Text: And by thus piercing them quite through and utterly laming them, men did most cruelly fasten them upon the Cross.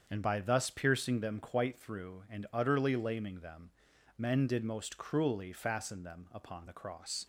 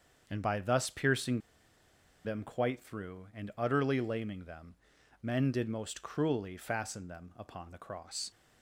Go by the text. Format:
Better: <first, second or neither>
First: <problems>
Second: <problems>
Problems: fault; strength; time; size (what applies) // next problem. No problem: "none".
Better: first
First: starts louder than the rest; until 1.0 s; 7 dB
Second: starts louder than the rest; strong; until 1.2 s; 7 dB // pauses between "piercing" and "them"; noticeable; at 1.4 s; 0.84 s long